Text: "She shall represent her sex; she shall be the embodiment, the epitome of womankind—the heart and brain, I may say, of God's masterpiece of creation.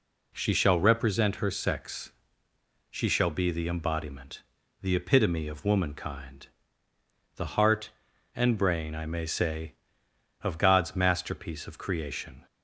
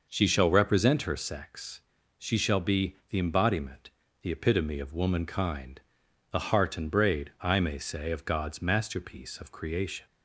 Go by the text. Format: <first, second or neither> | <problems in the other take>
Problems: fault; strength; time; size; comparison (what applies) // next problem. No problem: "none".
first | says "braid" for "brain"; at 6.8 s